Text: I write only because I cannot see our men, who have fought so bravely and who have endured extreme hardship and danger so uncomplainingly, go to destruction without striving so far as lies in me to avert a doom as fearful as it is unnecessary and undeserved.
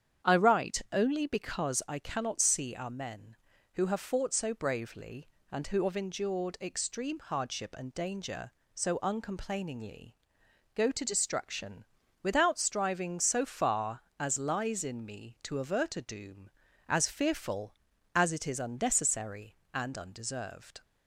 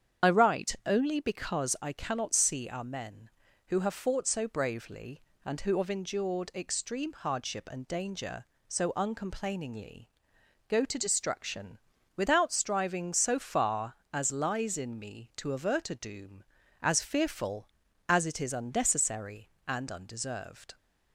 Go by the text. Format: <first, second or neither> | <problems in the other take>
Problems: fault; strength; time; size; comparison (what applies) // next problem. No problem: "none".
first | loses the start of "I"; at 0.2 s; 50 ms // starts louder than the rest; strong; until 1.3 s; 8.5 dB; strong in the first // pauses between "destruction" and "without"; at 11.7 s; 0.38 s long; also in the first